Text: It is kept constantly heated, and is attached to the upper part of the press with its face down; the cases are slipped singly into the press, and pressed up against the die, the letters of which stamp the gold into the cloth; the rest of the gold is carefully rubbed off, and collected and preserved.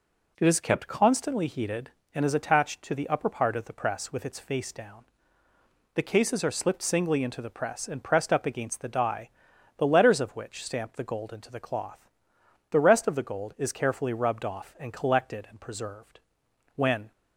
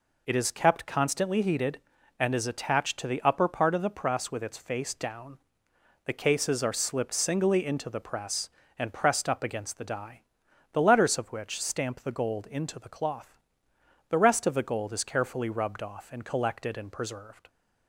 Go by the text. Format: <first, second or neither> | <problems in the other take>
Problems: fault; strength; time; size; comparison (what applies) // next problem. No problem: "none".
second | goes on to say "When"; slight; from 16.7 s on; 0.38 s long